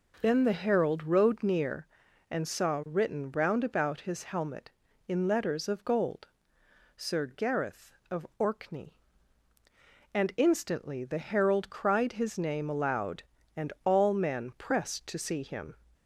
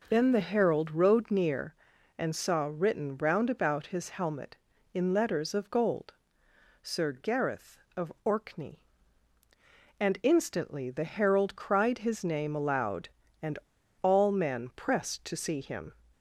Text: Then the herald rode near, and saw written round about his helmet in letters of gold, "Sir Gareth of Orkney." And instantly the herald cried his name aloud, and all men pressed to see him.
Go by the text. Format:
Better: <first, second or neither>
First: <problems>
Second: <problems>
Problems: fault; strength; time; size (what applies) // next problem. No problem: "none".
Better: first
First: none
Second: pauses between "and" and "all"; noticeable; at 13.5 s; 0.46 s long